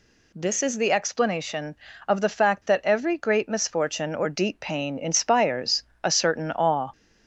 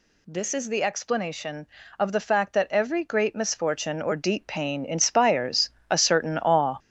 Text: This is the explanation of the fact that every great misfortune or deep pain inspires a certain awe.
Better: first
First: pauses between "inspires" and "a"; slight; at 5.8 s; 0.22 s long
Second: gets louder; strong; throughout; 9 dB // pauses between "inspires" and "a"; slight; at 5.6 s; 0.22 s long

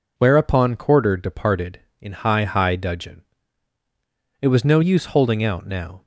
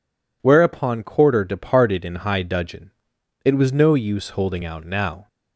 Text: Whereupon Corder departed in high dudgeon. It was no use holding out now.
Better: second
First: says "high" twice; at 2.4 s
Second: none

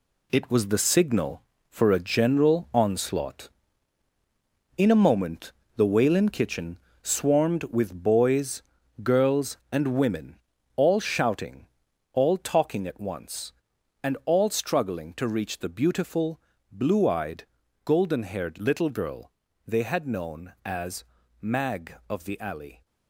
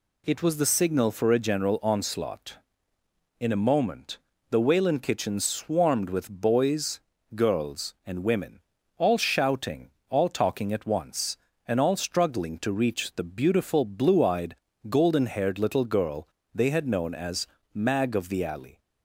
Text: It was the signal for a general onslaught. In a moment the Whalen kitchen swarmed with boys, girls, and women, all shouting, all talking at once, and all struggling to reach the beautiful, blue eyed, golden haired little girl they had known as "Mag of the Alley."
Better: second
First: gets quieter; strong; throughout; 7.5 dB // pauses between "moment" and "the"; slight; at 5.5 s; 0.24 s long // pauses between "kitchen" and "swarmed"; slight; at 6.7 s; 0.24 s long // pauses between "girl" and "they"; slight; at 19.3 s; 0.36 s long // pauses between "as" and "Mag"; at 21.0 s; 0.38 s long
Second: pauses between "moment" and "the"; slight; at 4.1 s; 0.32 s long // pauses between "girl" and "they"; slight; at 16.2 s; 0.28 s long // pauses between "as" and "Mag"; slight; at 17.4 s; 0.30 s long

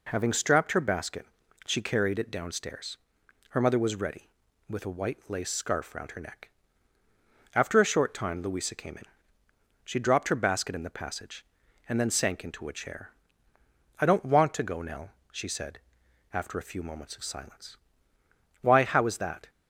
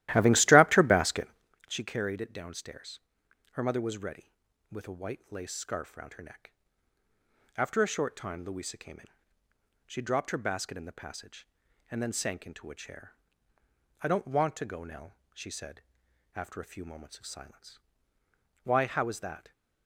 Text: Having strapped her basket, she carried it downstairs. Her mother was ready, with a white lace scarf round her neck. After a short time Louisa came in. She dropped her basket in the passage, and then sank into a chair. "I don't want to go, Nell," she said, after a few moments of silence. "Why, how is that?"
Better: first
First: none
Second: starts louder than the rest; strong; until 1.6 s; 15 dB

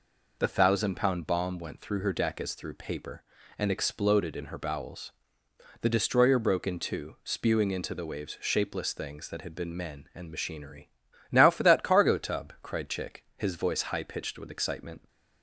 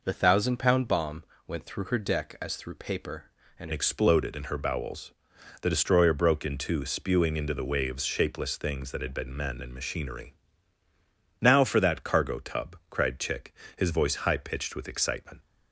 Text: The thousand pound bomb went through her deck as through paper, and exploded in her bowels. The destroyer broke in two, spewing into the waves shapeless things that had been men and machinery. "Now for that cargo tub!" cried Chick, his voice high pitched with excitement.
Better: first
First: none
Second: pauses between "bomb" and "went"; slight; at 1.2 s; 0.24 s long // changes voice at "exploded"; from 3.7 s on; 11.7 s long

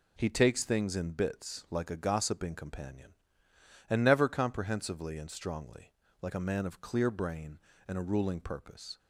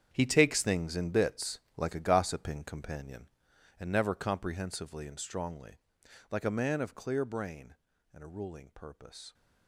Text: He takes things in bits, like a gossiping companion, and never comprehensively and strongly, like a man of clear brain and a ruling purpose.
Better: first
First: none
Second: gets quieter; strong; throughout; 13 dB

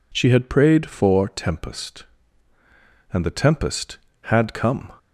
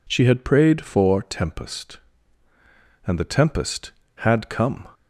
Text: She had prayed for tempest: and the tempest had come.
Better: neither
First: none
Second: none

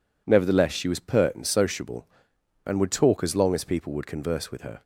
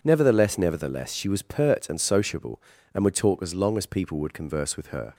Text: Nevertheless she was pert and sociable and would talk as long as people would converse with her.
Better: first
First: none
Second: says "Nevertheless" twice; at 0.5 s

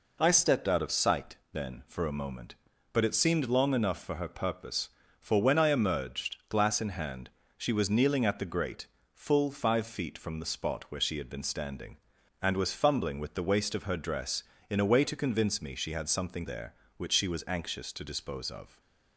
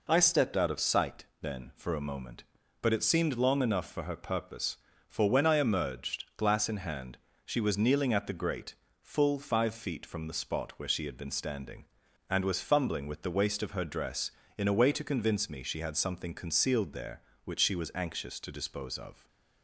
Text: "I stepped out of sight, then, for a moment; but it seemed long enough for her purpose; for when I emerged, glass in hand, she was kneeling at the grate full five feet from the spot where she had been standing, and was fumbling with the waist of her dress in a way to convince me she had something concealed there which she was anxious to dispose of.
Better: second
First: pauses between "grate" and "full"; slight; at 8.8 s; 0.26 s long // skips "concealed"; at 16.4 s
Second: pauses between "grate" and "full"; slight; at 8.7 s; 0.26 s long

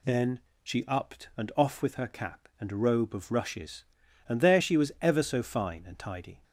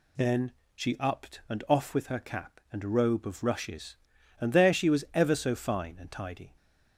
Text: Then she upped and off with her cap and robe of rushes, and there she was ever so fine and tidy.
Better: neither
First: pauses between "Then" and "she"; slight; at 0.4 s; 0.22 s long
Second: pauses between "Then" and "she"; slight; at 0.5 s; 0.22 s long

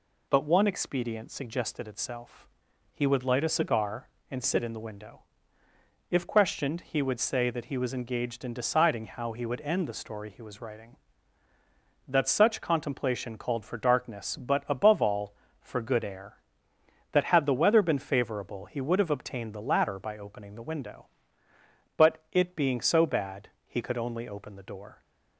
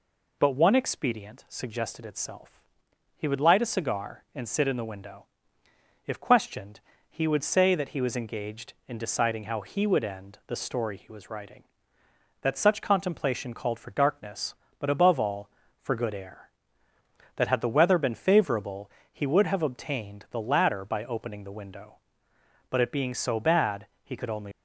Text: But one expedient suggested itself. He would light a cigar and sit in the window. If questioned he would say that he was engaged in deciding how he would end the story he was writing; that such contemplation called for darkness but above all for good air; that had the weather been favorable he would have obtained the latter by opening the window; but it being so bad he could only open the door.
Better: first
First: pauses between "bad" and "he"; slight; at 23.4 s; 0.18 s long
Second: pauses between "questioned" and "he"; slight; at 6.7 s; 0.30 s long // pauses between "favorable" and "he"; slight; at 18.9 s; 0.20 s long // pauses between "bad" and "he"; slight; at 23.8 s; 0.16 s long // stops before "open the door"; at 24.5 s

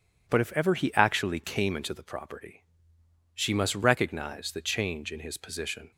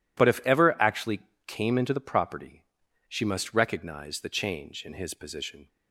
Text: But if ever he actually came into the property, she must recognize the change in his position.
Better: first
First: none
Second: skips "he"; at 0.7 s // pauses between "actually" and "came"; slight; at 1.1 s; 0.26 s long

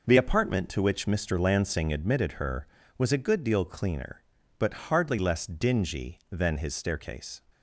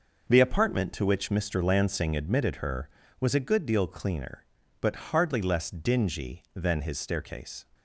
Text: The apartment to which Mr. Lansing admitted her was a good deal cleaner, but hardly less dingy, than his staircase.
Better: neither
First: none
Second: none

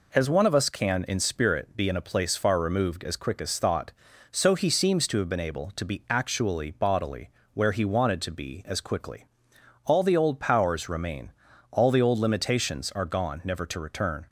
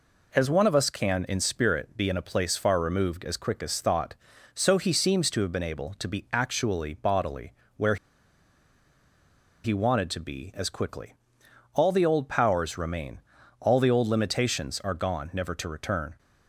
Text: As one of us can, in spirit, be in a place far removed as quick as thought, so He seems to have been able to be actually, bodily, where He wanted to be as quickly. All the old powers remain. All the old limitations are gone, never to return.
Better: first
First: none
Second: pauses between "where" and "He"; strong; at 7.9 s; 1.6 s long

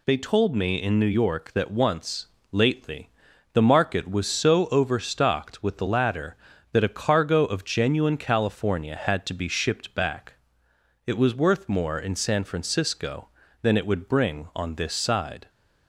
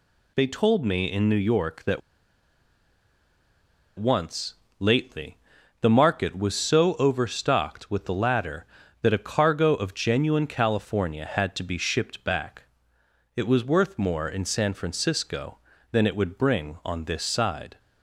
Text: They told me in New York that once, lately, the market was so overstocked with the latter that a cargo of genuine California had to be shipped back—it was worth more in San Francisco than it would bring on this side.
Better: first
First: none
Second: pauses between "that" and "once"; strong; at 2.0 s; 1.9 s long

